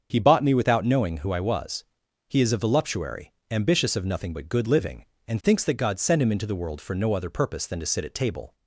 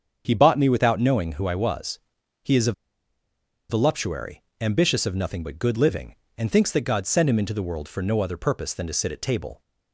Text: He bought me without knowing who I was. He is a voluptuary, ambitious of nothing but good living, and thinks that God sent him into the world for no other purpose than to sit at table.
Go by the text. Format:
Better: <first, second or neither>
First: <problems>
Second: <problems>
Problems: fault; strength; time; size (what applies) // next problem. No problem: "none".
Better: first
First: starts louder than the rest; until 1.1 s; 7 dB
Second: starts louder than the rest; strong; until 1.2 s; 7.5 dB // pauses between "a" and "voluptuary"; noticeable; at 2.7 s; 0.97 s long